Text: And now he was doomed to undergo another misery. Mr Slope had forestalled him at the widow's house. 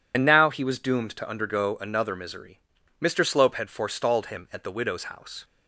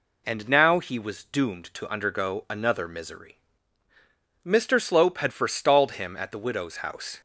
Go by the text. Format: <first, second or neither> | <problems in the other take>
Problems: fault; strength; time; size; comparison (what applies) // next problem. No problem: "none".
second | loses the start of "And"; at 0.1 s; 40 ms